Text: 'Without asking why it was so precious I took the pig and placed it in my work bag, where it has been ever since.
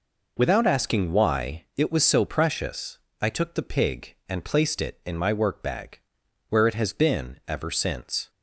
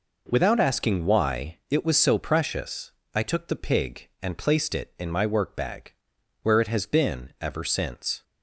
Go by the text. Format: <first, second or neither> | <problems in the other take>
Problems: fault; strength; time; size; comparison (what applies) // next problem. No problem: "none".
second | loses the start of "Without"; at 0.3 s; 40 ms // pauses between "precious" and "I"; slight; at 2.9 s; 0.24 s long; slight in the second